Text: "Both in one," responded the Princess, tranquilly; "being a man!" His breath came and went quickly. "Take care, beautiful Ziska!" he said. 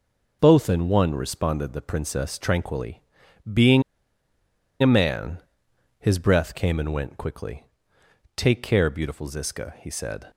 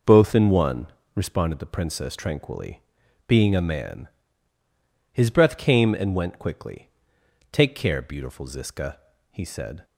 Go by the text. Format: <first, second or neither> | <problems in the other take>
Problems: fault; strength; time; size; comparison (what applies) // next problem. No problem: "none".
second | pauses between "being" and "a"; at 3.8 s; 0.99 s long